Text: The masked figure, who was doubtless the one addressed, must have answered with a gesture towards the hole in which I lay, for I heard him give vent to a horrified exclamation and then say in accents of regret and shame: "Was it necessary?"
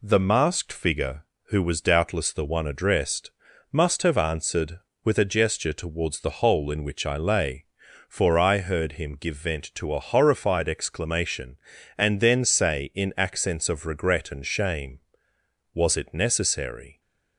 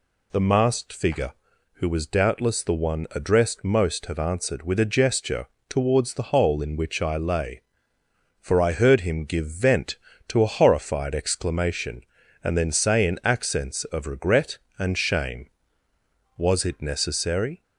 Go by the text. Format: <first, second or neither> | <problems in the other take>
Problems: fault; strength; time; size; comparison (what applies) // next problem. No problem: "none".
first | says "most" for "must"; at 3.6 s // pauses between "gesture" and "towards"; slight; at 5.4 s; 0.22 s long